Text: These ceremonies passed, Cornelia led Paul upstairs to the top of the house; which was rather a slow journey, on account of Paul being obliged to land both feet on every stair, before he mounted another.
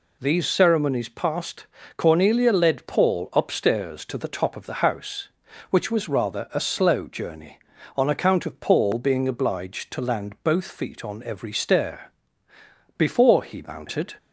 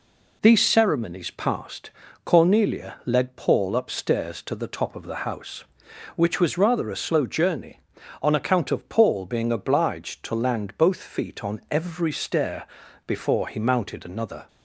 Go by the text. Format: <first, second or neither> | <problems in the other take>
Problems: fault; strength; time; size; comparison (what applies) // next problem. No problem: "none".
second | stops before "another"; at 14.1 s